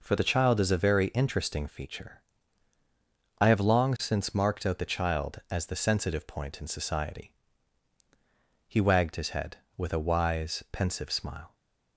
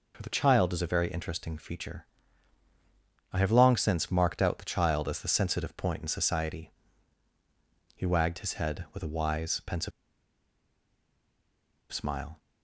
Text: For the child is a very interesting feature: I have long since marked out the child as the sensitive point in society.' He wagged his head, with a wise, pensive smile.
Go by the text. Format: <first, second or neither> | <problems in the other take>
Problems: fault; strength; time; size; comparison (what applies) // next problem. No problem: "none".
first | pauses between "pensive" and "smile"; strong; at 9.9 s; 2.0 s long